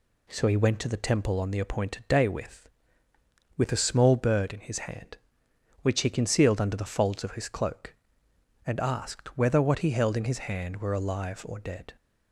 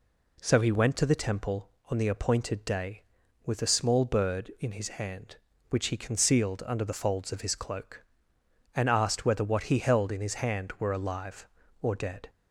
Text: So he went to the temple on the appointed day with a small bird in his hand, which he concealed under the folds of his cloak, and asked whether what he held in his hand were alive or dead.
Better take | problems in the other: second | says "with" twice; at 3.5 s

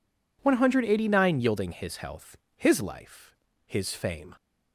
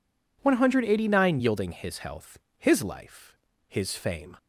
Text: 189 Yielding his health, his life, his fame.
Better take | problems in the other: neither | none

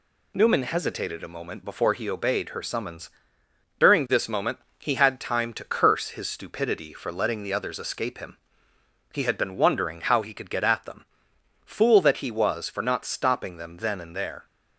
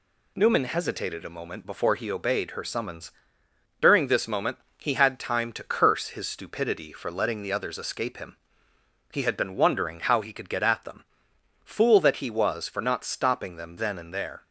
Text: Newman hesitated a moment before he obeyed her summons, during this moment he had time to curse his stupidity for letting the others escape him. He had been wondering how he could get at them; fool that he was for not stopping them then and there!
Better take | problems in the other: neither | pauses between "moment" and "he"; slight; the same in both

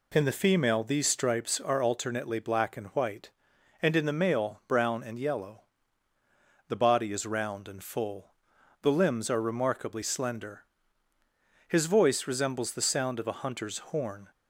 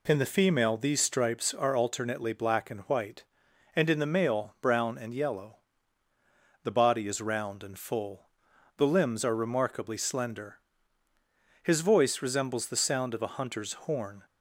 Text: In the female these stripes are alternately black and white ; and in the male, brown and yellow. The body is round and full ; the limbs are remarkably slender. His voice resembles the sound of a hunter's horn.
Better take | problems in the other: neither | none

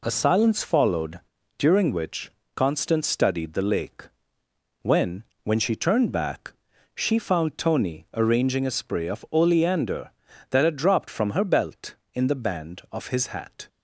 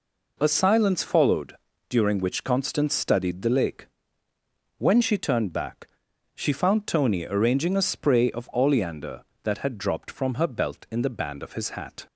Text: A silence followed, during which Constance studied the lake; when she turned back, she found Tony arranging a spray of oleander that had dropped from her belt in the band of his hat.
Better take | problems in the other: second | pauses between "which" and "Constance"; slight; at 2.2 s; 0.26 s long // says "when" twice; at 5.4 s

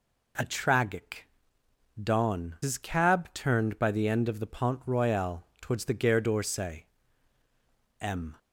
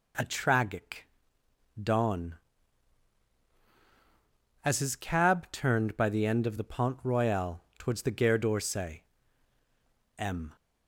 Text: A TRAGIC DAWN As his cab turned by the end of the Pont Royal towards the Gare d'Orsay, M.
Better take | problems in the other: second | pauses between "TRAGIC" and "DAWN"; noticeable; at 1.2 s; 0.74 s long; noticeable in the second // skips "As"; at 2.5 s // pauses between "Royal" and "towards"; slight; at 5.4 s; 0.18 s long; slight in the second

